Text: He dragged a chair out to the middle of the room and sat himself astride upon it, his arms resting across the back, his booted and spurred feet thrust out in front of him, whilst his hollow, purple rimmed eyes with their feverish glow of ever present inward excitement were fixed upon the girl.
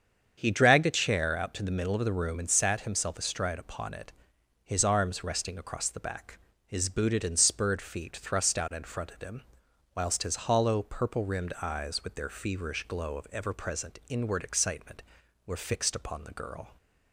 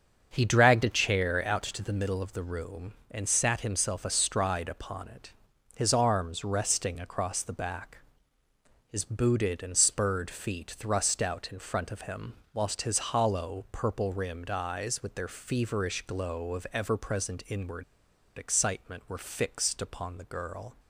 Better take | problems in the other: first | starts louder than the rest; until 1.3 s; 7 dB; strong in the first // pauses between "inward" and "excitement"; noticeable; at 17.8 s; 0.52 s long

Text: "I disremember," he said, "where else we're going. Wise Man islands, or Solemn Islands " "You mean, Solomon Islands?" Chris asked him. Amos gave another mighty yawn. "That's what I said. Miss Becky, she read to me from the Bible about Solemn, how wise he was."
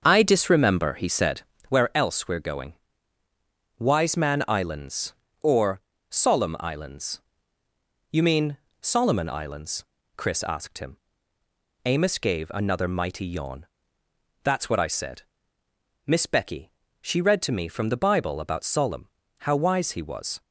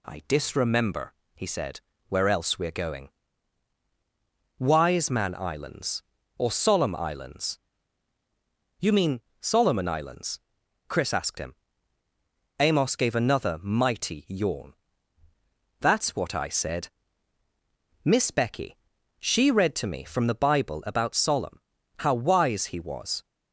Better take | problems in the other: second | starts louder than the rest; strong; until 1.7 s; 7 dB // pauses between "or" and "Solemn"; slight; at 5.7 s; 0.30 s long

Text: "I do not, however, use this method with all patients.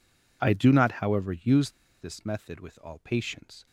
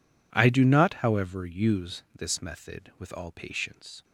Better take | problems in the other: second | pauses between "use" and "this"; slight; at 1.6 s; 0.31 s long

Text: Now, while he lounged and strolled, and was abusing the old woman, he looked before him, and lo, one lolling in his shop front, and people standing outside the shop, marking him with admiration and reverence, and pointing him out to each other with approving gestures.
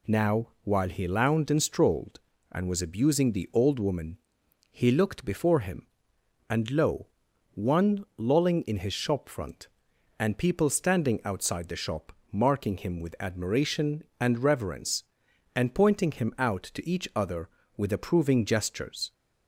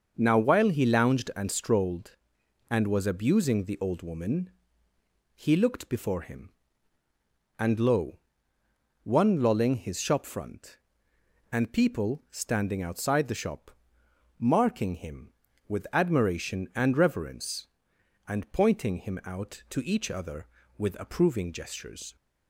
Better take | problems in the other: first | starts louder than the rest; until 1.1 s; 6.5 dB // skips "in"; at 9.7 s

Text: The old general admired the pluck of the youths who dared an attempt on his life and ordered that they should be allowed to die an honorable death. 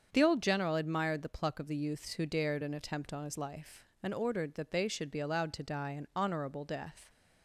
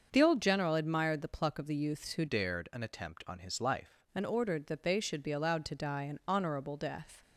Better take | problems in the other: first | starts louder than the rest; until 1.1 s; 6.5 dB; strong in the first // changes voice from "dared" to "life"; from 2.2 to 4.0 s; 1.8 s long

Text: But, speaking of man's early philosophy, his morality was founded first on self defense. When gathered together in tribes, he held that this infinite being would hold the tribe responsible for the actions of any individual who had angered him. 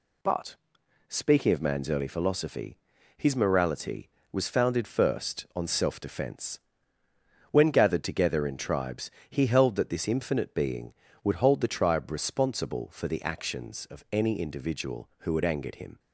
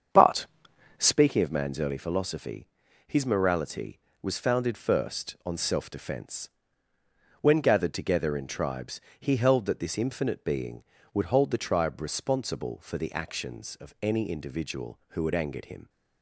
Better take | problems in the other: first | starts louder than the rest; strong; until 1.2 s; 7.5 dB

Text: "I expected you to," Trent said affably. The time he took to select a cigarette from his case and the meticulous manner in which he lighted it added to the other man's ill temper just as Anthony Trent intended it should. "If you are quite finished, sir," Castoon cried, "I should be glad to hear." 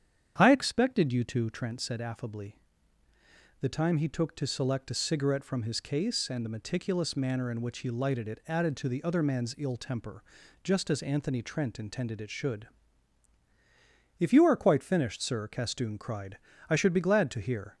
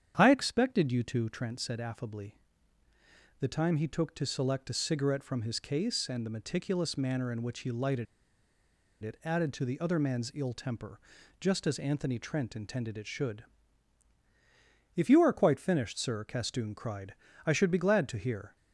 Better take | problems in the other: first | starts louder than the rest; strong; until 1.2 s; 8.5 dB; strong in the first // pauses between "lighted" and "it"; noticeable; at 8.0 s; 0.97 s long // pauses between "temper" and "just"; at 10.9 s; 0.42 s long; also in the first

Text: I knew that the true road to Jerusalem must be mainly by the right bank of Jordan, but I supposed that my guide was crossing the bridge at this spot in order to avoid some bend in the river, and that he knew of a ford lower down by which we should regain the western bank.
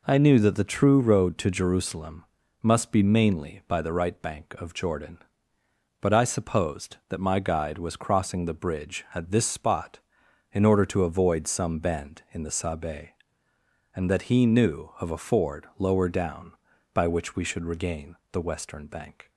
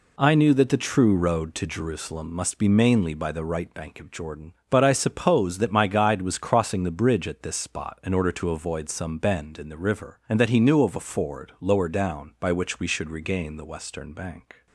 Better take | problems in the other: second | pauses between "Jerusalem" and "must"; slight; at 2.2 s; 0.36 s long // says "sabe" for "river"; at 12.5 s // pauses between "regain" and "the"; slight; at 18.1 s; 0.16 s long

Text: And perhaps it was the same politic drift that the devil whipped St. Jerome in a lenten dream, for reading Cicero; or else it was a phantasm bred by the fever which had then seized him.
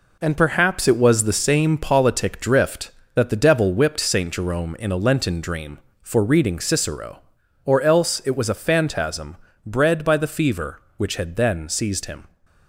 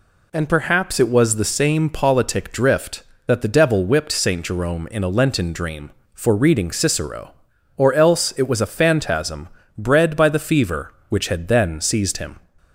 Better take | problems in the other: second | gets quieter; throughout; 7 dB // pauses between "phantasm" and "bred"; slight; at 9.3 s; 0.30 s long; slight in the second

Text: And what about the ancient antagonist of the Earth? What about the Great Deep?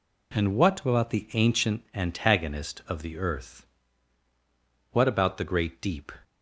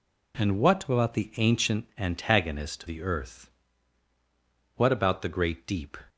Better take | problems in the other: first | skips "of"; at 2.8 s

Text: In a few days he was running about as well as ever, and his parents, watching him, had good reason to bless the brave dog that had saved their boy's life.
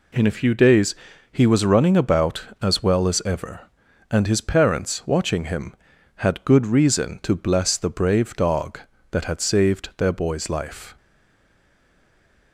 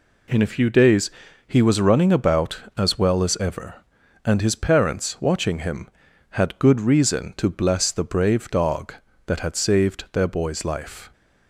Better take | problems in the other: second | pauses between "days" and "he"; at 0.9 s; 0.38 s long; also in the second // stays silent after the last word; noticeable; from 10.9 s on; 1.6 s long

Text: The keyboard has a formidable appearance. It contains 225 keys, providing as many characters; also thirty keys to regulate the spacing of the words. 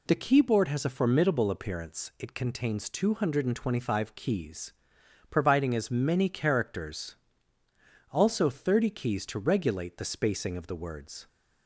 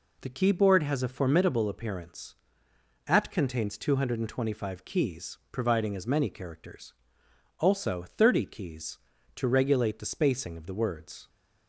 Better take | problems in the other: first | says "At" for "It"; at 3.0 s

